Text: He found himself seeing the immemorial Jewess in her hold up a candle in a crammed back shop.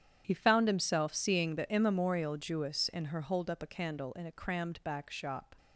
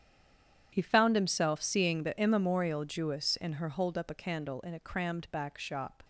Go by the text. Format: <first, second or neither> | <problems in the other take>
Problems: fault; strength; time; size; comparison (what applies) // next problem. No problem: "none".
first | stays silent before the first word; slight; until 0.7 s; 0.7 s long // starts louder than the rest; strong; until 1.7 s; 9.5 dB; strong in the first